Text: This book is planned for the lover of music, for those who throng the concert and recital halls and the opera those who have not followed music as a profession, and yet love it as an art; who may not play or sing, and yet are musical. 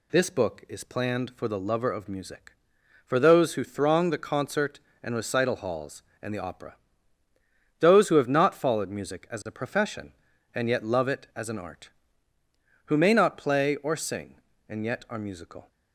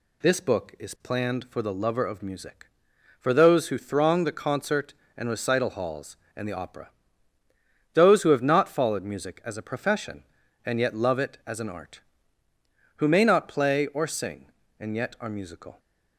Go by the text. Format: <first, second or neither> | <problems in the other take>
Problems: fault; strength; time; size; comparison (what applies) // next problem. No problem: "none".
neither | pauses between "opera" and "those"; the same in both